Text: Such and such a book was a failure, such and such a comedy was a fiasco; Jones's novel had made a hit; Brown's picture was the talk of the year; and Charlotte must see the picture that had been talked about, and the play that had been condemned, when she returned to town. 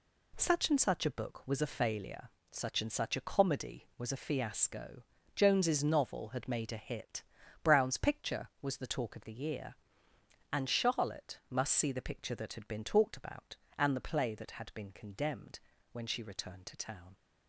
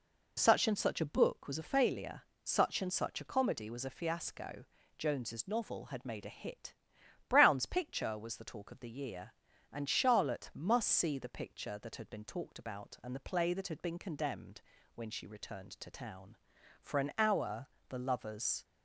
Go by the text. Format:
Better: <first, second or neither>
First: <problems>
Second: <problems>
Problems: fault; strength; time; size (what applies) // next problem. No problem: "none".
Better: first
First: none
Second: goes on to say "For an hour the lovers"; strong; from 16.8 s on; 1.8 s long